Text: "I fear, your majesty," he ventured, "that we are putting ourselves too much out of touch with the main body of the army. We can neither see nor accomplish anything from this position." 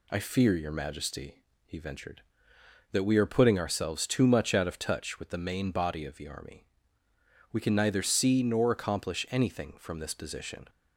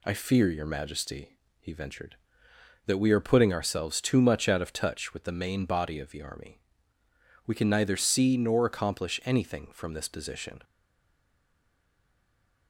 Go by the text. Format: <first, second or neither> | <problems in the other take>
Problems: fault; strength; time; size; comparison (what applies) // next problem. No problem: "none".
first | stays silent after the last word; noticeable; from 10.6 s on; 2.0 s long